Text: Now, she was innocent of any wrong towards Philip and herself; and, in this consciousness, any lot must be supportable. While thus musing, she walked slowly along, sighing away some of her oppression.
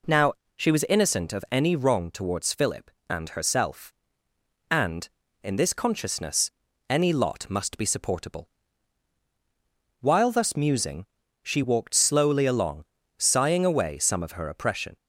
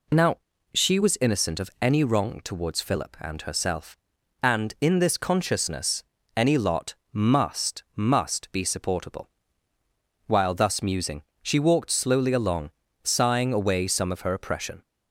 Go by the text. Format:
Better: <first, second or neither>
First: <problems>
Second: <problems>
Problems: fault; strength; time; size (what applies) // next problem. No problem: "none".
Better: first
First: none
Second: pauses between "lot" and "must"; slight; at 6.9 s; 0.16 s long // says "must" twice; at 7.9 s